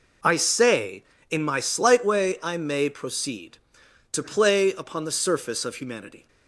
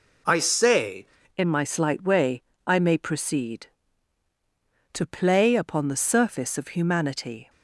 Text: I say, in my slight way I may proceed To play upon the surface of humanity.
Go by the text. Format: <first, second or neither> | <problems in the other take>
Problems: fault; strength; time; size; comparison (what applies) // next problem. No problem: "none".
first | changes voice at "in"; from 1.3 s on; 6.1 s long // pauses between "way" and "I"; slight; at 2.4 s; 0.24 s long